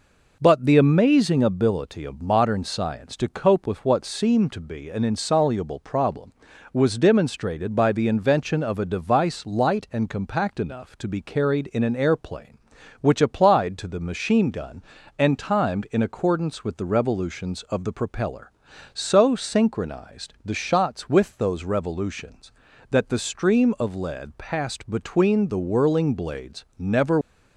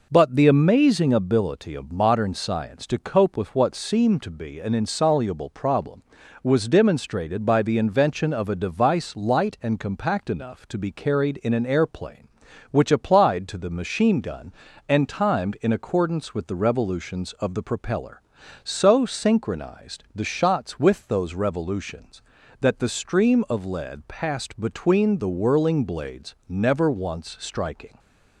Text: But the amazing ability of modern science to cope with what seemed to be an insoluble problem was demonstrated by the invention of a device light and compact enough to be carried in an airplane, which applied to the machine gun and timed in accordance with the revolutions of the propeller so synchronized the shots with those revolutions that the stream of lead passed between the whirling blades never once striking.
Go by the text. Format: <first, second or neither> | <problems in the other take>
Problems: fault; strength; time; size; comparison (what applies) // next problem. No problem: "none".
second | stops before "once striking"; at 27.2 s